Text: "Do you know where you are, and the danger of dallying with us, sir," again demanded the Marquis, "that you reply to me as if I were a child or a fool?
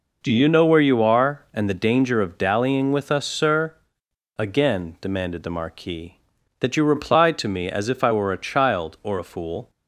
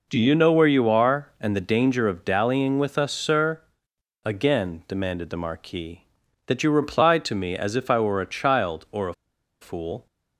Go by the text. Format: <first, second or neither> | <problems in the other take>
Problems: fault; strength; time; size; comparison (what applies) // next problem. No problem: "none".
first | pauses between "a" and "fool"; noticeable; at 9.1 s; 0.47 s long